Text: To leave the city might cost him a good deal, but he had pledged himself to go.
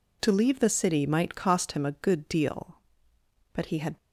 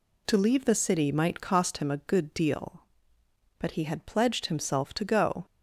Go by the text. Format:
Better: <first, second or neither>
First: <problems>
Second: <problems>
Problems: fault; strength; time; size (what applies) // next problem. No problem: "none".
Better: second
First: stops before "pledged himself to go"; at 3.9 s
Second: none